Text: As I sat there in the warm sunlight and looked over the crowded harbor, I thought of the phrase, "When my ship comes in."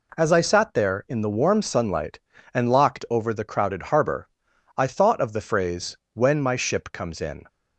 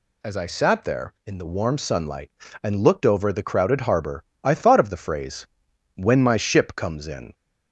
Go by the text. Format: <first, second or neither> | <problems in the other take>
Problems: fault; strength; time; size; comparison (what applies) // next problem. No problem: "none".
second | says "locked" for "looked"; at 2.6 s